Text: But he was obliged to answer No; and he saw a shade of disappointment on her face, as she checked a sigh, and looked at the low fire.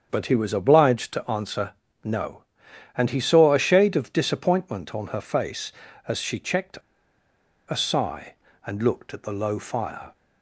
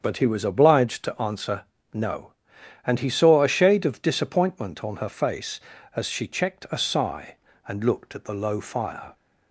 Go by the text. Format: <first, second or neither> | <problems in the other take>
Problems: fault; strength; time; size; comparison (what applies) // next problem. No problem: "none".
second | starts louder than the rest; strong; until 1.1 s; 7.5 dB; strong in the second // pauses between "answer" and "No"; slight; at 1.7 s; 0.32 s long; slight in the second // pauses between "checked" and "a"; noticeable; at 6.7 s; 0.90 s long